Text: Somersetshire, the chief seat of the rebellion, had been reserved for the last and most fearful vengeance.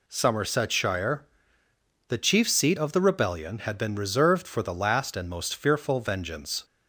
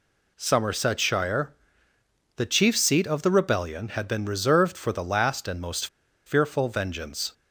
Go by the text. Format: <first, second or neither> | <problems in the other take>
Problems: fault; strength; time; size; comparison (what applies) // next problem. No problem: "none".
first | pauses between "most" and "fearful"; at 5.8 s; 0.39 s long